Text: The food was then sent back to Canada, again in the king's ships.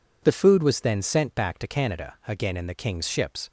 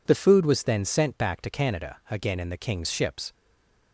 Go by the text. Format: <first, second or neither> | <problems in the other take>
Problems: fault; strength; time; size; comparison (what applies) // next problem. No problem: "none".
first | stays silent after the last word; slight; from 3.3 s on; 0.6 s long